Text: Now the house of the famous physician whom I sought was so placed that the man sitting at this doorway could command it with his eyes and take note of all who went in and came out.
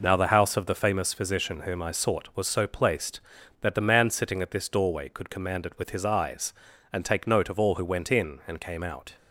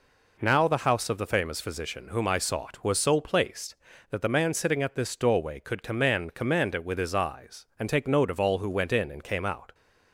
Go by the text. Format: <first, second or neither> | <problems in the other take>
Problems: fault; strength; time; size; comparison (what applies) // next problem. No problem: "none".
first | says "command" twice; at 6.3 s